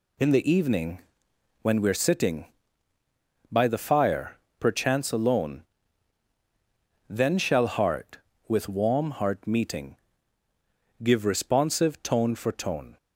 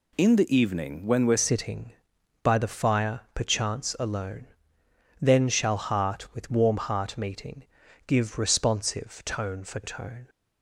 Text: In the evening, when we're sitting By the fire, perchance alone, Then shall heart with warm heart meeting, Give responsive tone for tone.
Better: first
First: none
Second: changes voice at "sitting"; from 1.3 s on; 8.9 s long

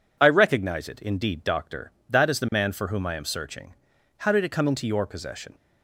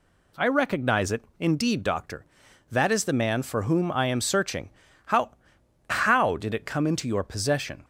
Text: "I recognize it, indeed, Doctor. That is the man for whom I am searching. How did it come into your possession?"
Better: first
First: none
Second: says "How" twice; at 5.8 s

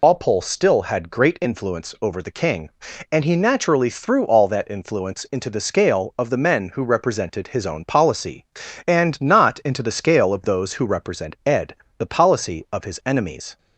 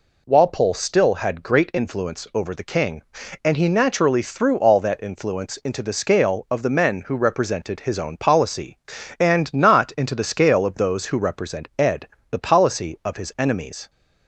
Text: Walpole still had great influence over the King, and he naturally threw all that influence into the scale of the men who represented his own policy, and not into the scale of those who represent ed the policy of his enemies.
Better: second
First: loses the start of "Walpole"; at 0.0 s; 95 ms // pauses between "ed" and "the"; slight; at 11.7 s; 0.22 s long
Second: pauses between "ed" and "the"; slight; at 12.0 s; 0.22 s long

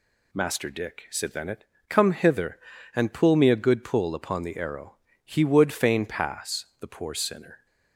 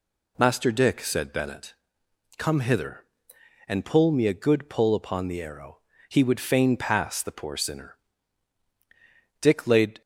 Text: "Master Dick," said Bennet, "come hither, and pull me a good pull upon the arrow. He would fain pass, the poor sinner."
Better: first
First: none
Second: goes on to say "Dick laid"; noticeable; from 9.3 s on; 0.62 s long

